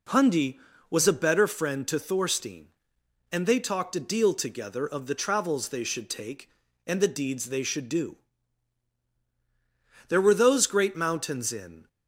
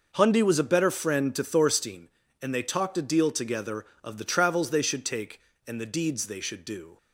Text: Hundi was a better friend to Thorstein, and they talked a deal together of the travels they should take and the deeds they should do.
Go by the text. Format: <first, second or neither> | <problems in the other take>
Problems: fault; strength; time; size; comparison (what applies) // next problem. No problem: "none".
second | goes on to say "There were those great mountains in"; strong; from 10.0 s on; 1.8 s long